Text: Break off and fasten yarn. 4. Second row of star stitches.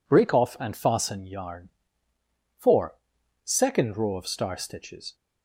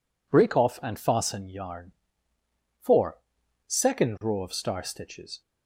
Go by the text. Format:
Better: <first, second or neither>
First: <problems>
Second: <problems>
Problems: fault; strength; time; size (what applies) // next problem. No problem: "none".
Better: neither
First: none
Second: none